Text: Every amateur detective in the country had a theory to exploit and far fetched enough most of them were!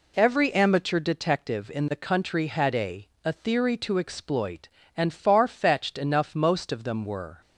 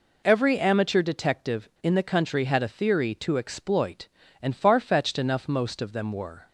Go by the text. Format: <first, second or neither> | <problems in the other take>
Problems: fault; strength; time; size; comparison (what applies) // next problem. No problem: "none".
second | says "a" twice; at 3.2 s